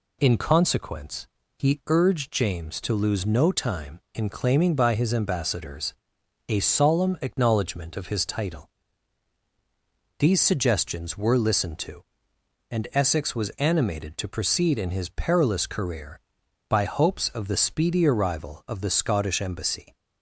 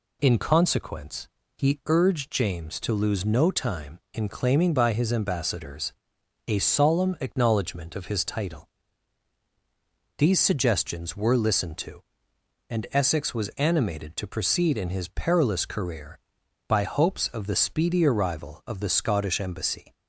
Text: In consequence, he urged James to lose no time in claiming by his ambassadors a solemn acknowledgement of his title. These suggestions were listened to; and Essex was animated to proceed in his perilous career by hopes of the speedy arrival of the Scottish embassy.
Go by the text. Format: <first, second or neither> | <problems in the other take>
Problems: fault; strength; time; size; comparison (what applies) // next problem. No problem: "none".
neither | pauses between "ambassadors" and "a"; noticeable; the same in both